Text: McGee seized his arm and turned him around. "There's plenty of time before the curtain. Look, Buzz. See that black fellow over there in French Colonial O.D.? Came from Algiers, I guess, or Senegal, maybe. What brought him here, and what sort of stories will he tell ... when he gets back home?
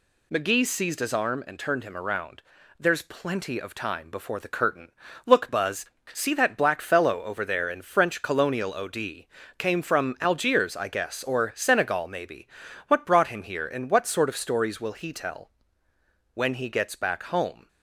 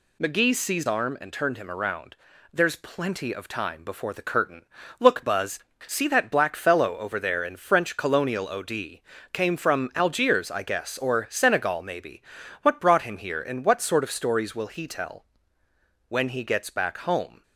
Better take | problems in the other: first | skips "his"; at 0.8 s

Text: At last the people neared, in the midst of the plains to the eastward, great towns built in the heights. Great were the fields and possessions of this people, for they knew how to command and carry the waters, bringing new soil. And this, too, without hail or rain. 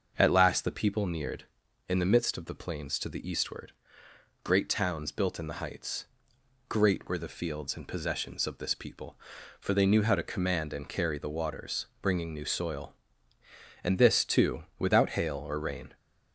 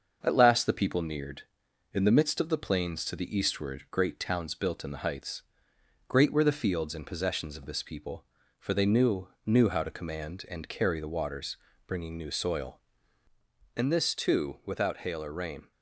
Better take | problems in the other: first | starts louder than the rest; until 1.2 s; 6.5 dB; also in the first // says "knew" twice; at 9.4 s

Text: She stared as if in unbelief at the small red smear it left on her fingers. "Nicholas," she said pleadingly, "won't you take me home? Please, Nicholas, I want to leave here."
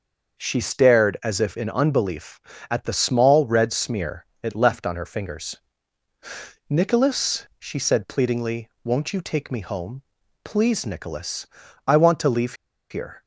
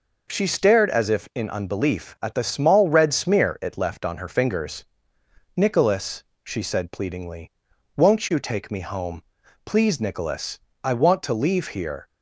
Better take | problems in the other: second | starts louder than the rest; until 1.4 s; 6 dB // pauses between "smear" and "it"; slight; at 4.2 s; 0.16 s long // pauses between "leave" and "here"; at 12.5 s; 0.37 s long

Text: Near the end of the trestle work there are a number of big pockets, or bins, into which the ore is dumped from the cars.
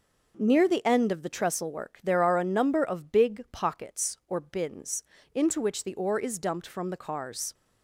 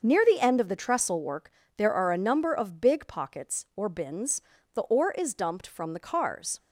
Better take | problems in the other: first | starts louder than the rest; until 1.0 s; 6 dB // pauses between "work" and "there"; slight; at 1.5 s; 0.26 s long // skips "into which"; at 4.5 s

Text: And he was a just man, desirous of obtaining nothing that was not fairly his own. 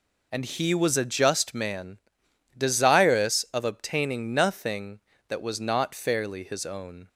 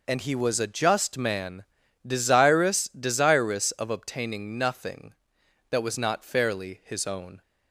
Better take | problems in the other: first | says "desirous" twice; at 2.9 s

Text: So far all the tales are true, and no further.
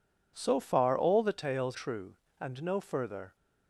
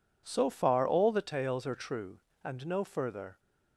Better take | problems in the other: second | skips "are"; at 1.7 s

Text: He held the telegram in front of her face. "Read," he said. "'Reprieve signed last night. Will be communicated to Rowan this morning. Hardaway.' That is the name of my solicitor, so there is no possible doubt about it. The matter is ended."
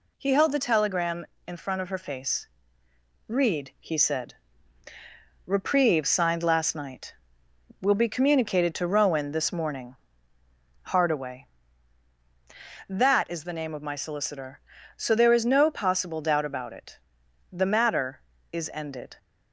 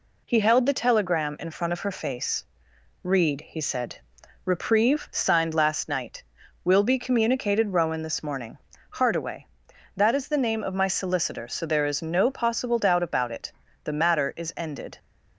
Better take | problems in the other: first | skips "to"; at 7.7 s

